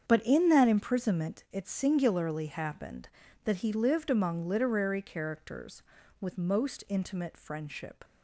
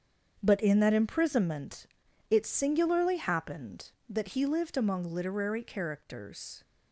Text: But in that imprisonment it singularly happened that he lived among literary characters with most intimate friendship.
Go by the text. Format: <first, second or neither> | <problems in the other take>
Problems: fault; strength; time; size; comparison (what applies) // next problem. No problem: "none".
first | starts louder than the rest; strong; until 1.4 s; 7.5 dB; strong in the first // pauses between "imprisonment" and "it"; at 1.8 s; 0.42 s long // stops before "with most intimate friendship"; at 6.6 s